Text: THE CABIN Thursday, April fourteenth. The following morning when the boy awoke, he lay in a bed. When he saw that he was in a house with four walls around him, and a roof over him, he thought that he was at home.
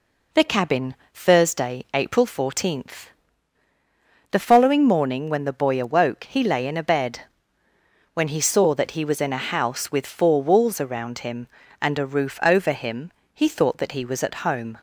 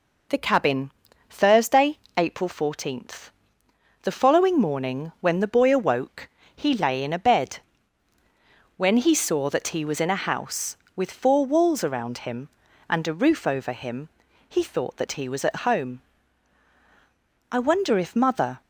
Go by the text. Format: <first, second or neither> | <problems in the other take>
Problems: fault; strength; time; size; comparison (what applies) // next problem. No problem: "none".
first | pauses between "CABIN" and "Thursday"; at 0.9 s; 0.38 s long; slight in the first // goes on to say "I wonder if mother"; noticeable; from 17.5 s on; 1.1 s long